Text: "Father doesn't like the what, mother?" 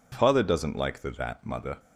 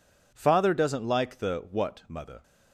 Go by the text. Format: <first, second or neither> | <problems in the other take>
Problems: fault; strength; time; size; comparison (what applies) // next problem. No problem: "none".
second | says "that" for "what"; at 1.0 s